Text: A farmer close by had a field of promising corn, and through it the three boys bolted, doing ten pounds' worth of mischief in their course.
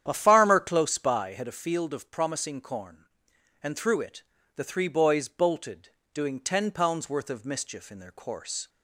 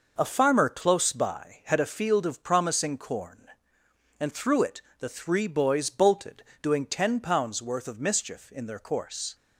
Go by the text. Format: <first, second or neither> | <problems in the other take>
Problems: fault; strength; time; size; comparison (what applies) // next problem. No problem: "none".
second | starts louder than the rest; strong; until 1.4 s; 9.5 dB // pauses between "it" and "the"; slight; at 4.2 s; 0.32 s long; slight in the second